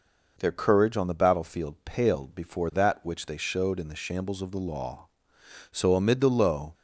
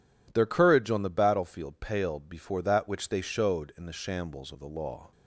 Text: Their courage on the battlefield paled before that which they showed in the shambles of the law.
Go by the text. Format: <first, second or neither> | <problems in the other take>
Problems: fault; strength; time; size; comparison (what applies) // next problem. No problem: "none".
second | goes on to say "So amid the low"; noticeable; from 5.7 s on; 1.0 s long